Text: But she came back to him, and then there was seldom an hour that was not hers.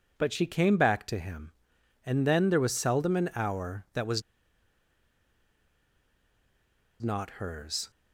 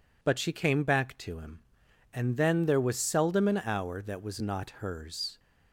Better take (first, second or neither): second